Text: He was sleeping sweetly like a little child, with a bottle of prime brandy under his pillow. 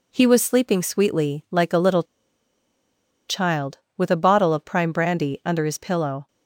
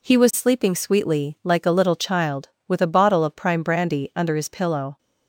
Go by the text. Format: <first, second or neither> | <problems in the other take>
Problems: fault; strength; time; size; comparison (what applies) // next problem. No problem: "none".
second | pauses between "little" and "child"; strong; at 2.0 s; 1.2 s long